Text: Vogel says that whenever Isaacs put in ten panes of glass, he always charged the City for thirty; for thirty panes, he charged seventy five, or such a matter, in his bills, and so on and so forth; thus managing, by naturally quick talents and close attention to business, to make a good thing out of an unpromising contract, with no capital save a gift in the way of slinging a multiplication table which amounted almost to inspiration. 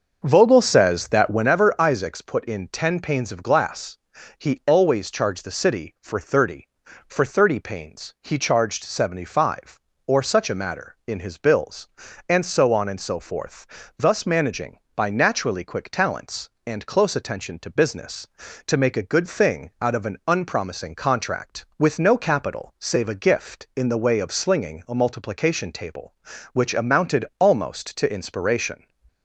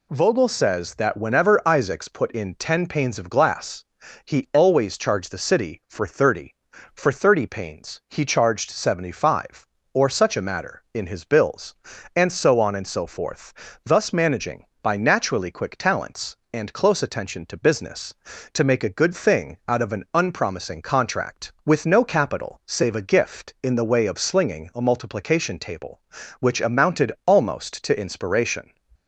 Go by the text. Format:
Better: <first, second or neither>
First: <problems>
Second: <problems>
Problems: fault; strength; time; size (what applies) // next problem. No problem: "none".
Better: second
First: starts louder than the rest; until 1.5 s; 6.5 dB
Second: none